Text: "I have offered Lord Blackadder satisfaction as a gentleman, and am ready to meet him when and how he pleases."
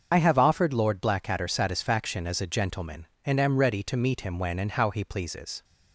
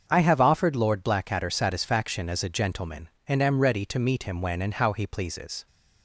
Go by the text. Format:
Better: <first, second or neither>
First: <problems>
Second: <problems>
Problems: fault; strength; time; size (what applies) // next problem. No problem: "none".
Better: second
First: loses the start of "I"; at 0.1 s; 50 ms // starts louder than the rest; until 1.1 s; 6.5 dB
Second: starts louder than the rest; until 1.1 s; 6.5 dB